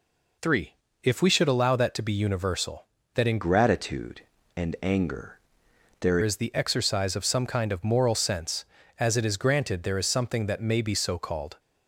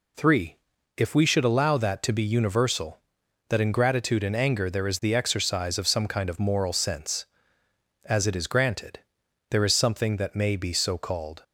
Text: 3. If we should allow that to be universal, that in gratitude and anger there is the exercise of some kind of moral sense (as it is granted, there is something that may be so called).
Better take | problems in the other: second | changes voice from "gratitude" to "there"; from 3.4 to 6.1 s; 2.7 s long // pauses between "anger" and "there"; noticeable; at 5.3 s; 0.64 s long

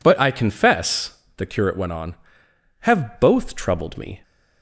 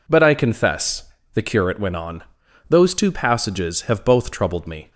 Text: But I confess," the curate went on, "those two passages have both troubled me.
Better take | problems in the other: second | skips "those two passages"; at 2.4 s

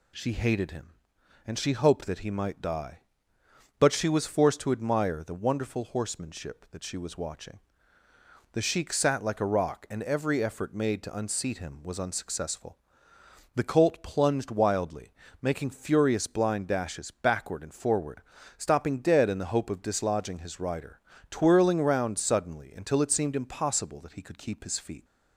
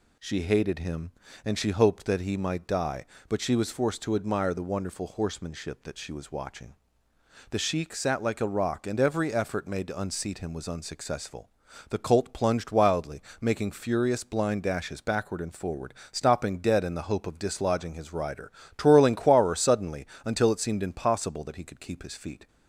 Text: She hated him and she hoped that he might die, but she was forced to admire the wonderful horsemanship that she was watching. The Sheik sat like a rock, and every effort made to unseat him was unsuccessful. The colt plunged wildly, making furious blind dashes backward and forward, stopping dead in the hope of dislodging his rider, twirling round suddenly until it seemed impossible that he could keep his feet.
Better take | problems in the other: first | says "quarer" for "round"; at 19.1 s // pauses between "suddenly" and "until"; slight; at 20.0 s; 0.20 s long

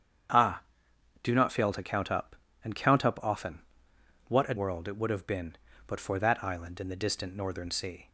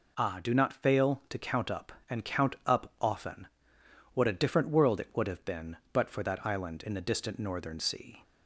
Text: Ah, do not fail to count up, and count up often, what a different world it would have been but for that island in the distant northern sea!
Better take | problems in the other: second | starts louder than the rest; strong; until 1.9 s; 8 dB // skips "different"; at 4.5 s

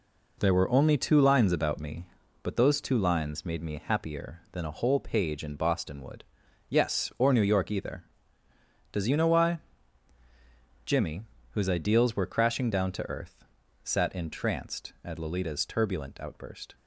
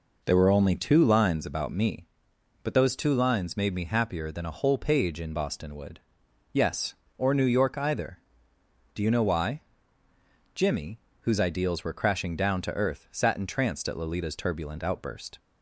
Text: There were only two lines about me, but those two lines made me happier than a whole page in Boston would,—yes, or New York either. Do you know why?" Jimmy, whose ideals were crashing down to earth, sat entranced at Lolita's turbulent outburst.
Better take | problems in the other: second | says "Does" for "Do"; at 8.9 s

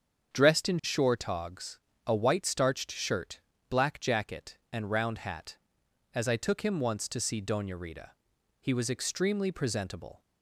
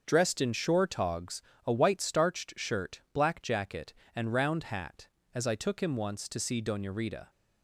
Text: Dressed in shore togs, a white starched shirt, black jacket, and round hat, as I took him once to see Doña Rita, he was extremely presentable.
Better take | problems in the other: first | starts louder than the rest; until 1.0 s; 6.5 dB; strong in the first // stops before "he was extremely presentable"; at 7.2 s

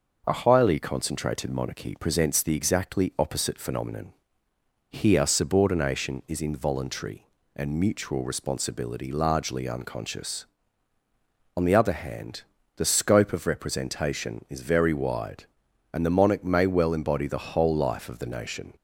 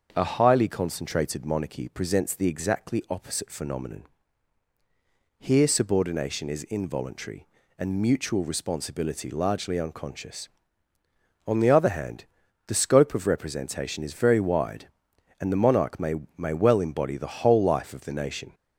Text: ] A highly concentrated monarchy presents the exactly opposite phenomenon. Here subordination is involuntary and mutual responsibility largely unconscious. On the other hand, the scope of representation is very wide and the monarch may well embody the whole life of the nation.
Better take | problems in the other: first | starts louder than the rest; until 1.1 s; 6.5 dB // says "may" twice; at 16.3 s

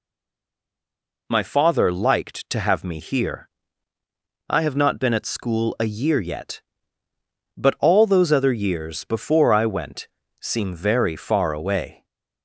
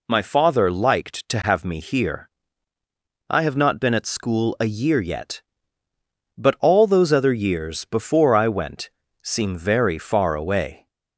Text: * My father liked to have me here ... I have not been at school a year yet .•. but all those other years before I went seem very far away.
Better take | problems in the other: second | stays silent before the first word; noticeable; until 1.2 s; 1.2 s long // pauses between "went" and "seem"; slight; at 10.0 s; 0.34 s long; slight in the second

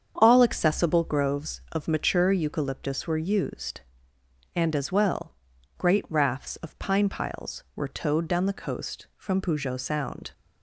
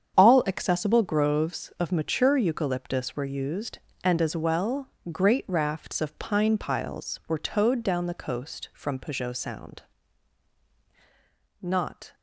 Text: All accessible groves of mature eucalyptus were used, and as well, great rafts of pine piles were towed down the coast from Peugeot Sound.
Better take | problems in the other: first | starts louder than the rest; strong; until 1.1 s; 8 dB; strong in the first // goes on to say "Not"; from 11.6 s on; 0.54 s long

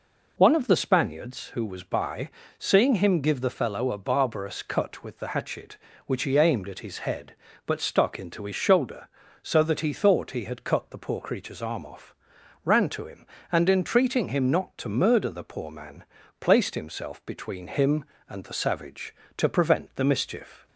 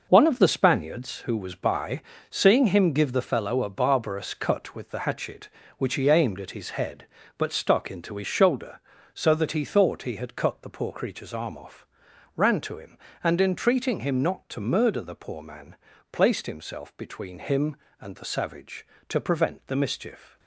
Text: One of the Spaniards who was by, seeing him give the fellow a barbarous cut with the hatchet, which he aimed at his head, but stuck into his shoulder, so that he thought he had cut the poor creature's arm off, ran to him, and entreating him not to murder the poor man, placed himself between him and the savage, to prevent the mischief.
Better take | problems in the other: first | gets quieter; strong; throughout; 9 dB

